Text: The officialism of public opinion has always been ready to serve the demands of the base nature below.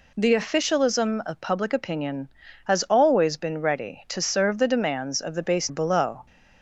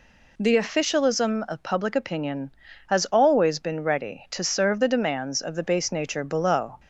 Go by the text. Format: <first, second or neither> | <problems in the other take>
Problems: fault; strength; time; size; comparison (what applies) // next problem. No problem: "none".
second | skips "nature"; at 5.6 s